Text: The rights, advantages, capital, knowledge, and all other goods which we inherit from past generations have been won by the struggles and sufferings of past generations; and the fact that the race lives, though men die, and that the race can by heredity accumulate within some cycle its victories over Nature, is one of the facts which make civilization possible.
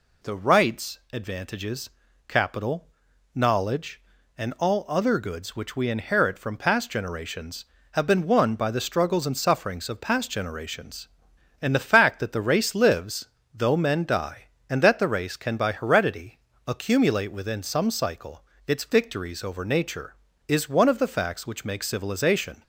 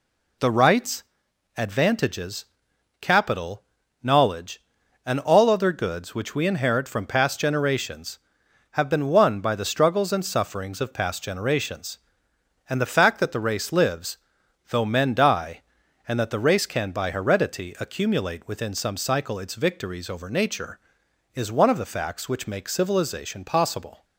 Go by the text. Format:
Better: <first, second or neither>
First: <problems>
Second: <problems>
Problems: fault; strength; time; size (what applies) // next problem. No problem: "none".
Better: second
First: pauses between "heredity" and "accumulate"; slight; at 16.3 s; 0.30 s long // pauses between "cycle" and "its"; slight; at 18.4 s; 0.20 s long // stops before "possible"; at 22.6 s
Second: none